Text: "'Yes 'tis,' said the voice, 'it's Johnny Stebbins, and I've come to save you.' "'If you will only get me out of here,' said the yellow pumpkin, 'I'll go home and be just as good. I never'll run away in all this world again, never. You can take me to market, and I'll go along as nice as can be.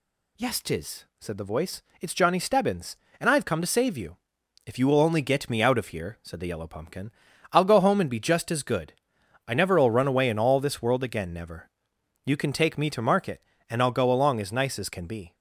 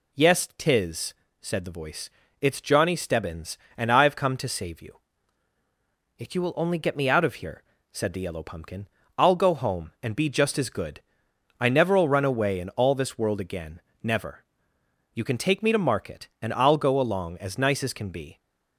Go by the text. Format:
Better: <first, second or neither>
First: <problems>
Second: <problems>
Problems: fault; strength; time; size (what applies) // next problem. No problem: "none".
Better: neither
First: none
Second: none